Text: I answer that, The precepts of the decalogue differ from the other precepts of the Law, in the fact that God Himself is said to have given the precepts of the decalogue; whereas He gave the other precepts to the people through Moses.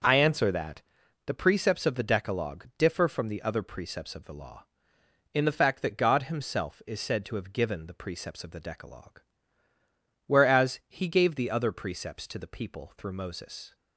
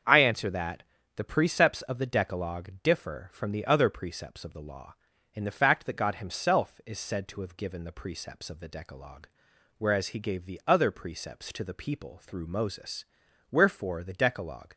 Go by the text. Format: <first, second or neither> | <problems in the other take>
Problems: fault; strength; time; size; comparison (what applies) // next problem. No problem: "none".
first | starts louder than the rest; until 1.3 s; 7 dB; noticeable in the first // goes on to say "Wherefore the decalogue"; noticeable; from 13.5 s on; 1.2 s long